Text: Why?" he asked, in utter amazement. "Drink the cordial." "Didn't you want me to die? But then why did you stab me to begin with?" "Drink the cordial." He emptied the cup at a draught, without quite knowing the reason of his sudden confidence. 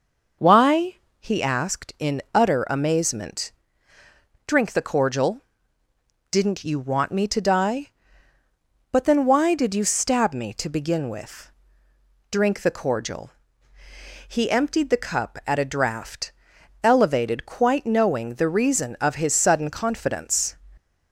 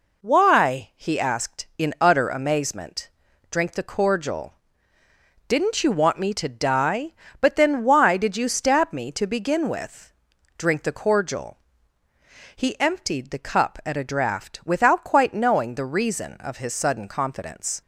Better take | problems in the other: second | says "elevated" for "without"; at 16.8 s

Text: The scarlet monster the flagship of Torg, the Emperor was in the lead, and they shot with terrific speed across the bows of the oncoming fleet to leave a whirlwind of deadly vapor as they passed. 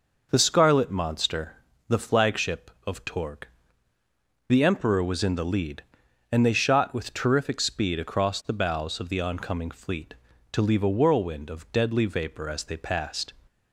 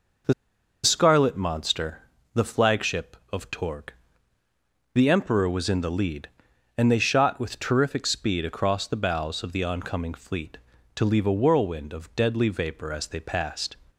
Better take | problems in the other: first | pauses between "The" and "scarlet"; noticeable; at 0.3 s; 0.50 s long // pauses between "monster" and "the"; slight; at 2.0 s; 0.32 s long; slight in the first

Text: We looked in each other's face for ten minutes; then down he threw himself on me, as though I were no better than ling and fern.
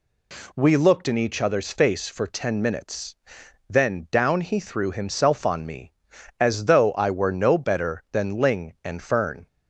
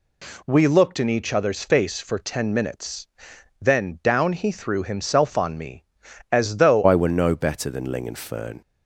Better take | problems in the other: first | changes voice at "I"; from 6.8 s on; 1.7 s long

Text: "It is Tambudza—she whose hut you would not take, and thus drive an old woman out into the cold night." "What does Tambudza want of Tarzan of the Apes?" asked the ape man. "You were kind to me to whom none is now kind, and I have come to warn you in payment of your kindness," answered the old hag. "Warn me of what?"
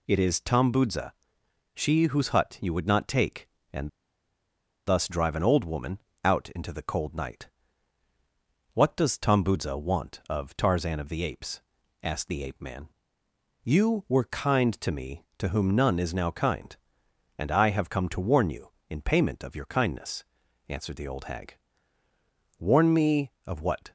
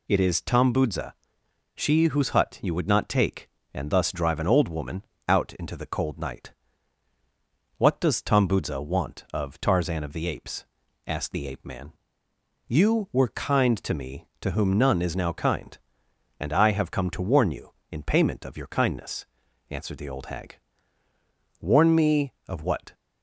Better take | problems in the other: second | pauses between "and" and "thus"; noticeable; at 3.8 s; 0.97 s long // pauses between "woman" and "out"; slight; at 6.0 s; 0.24 s long; slight in the second

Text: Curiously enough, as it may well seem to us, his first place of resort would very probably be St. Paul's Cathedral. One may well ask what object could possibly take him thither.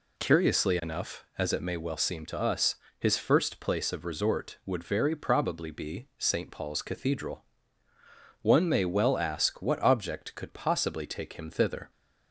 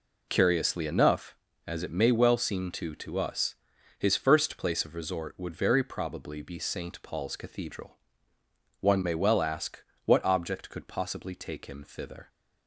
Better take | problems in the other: first | says "to" twice; at 2.9 s // pauses between "ask" and "what"; slight; at 9.8 s; 0.22 s long

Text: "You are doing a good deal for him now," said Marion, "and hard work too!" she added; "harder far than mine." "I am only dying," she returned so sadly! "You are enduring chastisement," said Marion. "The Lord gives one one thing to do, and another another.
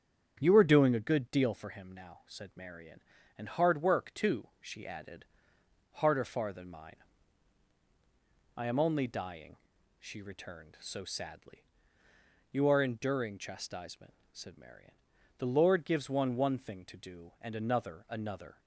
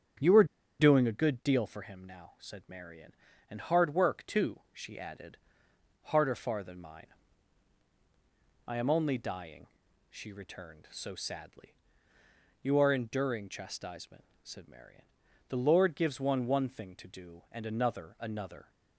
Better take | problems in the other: first | starts louder than the rest; strong; until 1.5 s; 8 dB; strong in the first // pauses between "are" and "doing"; slight; at 0.4 s; 0.35 s long

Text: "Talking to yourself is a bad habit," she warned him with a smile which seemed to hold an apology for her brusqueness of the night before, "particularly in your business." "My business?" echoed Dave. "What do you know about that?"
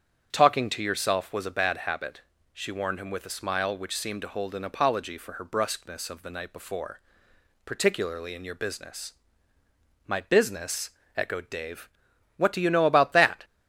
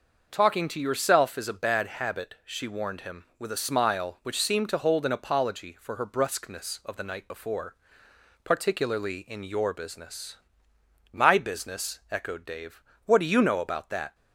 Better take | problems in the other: second | starts louder than the rest; strong; until 1.3 s; 8 dB; noticeable in the second // says "was" for "is"; at 1.3 s

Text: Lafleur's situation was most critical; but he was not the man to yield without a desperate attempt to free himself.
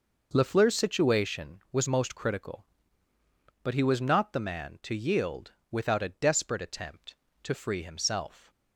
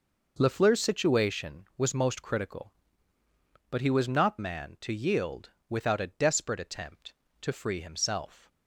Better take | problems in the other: first | skips "the"; at 4.3 s // pauses between "yield" and "without"; slight; at 5.4 s; 0.22 s long; slight in the first

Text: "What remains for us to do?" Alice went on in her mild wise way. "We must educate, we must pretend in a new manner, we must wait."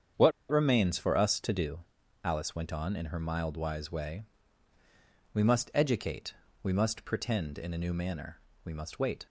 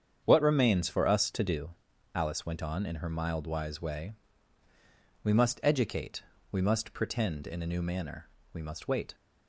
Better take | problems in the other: second | starts louder than the rest; strong; until 1.3 s; 8 dB; strong in the second // pauses between "What" and "remains"; slight; at 0.3 s; 0.20 s long

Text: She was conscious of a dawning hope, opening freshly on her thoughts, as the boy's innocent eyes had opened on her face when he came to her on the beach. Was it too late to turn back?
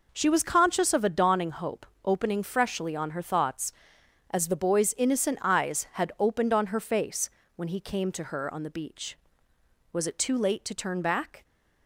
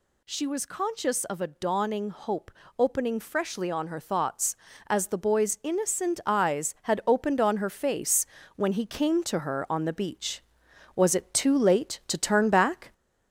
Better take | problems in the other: first | gets louder; slight; throughout; 2.5 dB // pauses between "face" and "when"; slight; at 8.2 s; 0.30 s long; slight in the first

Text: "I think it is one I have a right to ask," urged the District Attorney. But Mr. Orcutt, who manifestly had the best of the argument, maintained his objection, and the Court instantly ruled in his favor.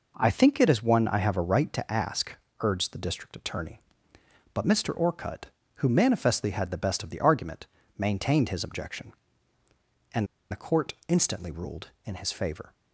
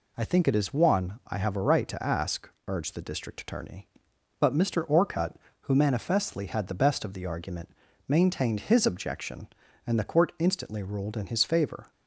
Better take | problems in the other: second | pauses between "and" and "the"; slight; at 10.2 s; 0.25 s long // pauses between "Court" and "instantly"; slight; at 10.9 s; 0.16 s long

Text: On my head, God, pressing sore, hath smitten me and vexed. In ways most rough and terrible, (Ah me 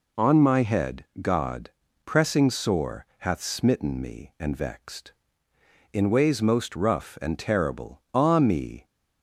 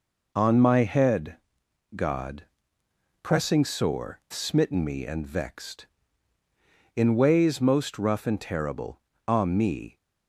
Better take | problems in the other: first | skips "hath"; at 4.2 s

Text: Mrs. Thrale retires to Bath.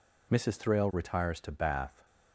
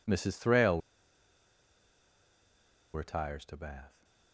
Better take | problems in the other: first | pauses between "Thrale" and "retires"; strong; at 0.8 s; 2.1 s long

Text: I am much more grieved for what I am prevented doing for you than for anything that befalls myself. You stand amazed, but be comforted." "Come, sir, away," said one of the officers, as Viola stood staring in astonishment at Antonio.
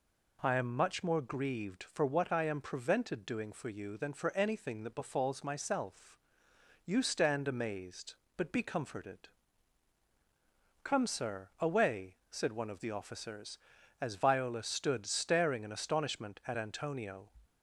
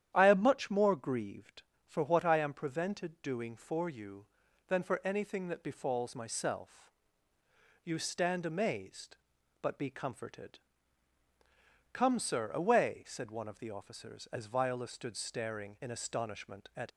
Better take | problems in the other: first | starts louder than the rest; strong; until 1.1 s; 10.5 dB // stops before "Antonio"; at 16.9 s

